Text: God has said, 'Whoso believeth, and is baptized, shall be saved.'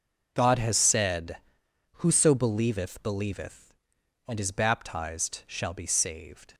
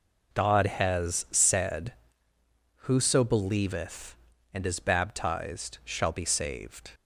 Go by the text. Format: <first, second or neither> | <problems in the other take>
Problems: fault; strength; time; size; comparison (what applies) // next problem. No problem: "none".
second | says "believeth" twice; at 3.0 s